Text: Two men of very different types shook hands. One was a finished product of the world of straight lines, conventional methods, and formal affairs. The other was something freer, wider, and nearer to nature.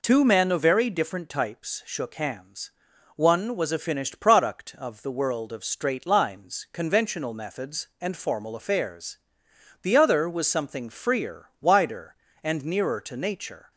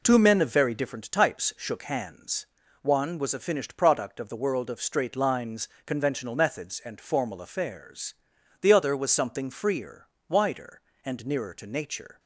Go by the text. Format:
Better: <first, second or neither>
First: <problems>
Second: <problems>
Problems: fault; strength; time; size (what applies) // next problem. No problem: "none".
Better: neither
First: none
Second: none